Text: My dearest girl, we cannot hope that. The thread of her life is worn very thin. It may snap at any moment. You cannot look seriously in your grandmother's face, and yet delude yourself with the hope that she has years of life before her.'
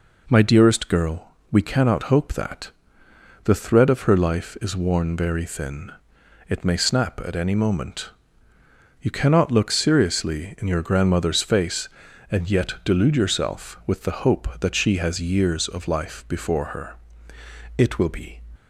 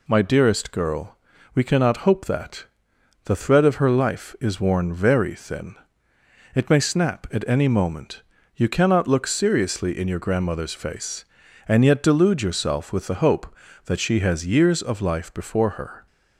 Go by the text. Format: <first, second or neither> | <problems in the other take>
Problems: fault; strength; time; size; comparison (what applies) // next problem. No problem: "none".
second | goes on to say "It will be"; noticeable; from 17.7 s on; 0.64 s long